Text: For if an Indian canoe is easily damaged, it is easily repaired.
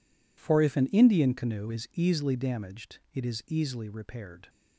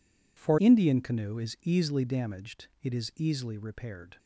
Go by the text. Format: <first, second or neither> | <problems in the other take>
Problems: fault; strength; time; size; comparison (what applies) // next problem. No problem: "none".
first | skips "if an"; at 0.5 s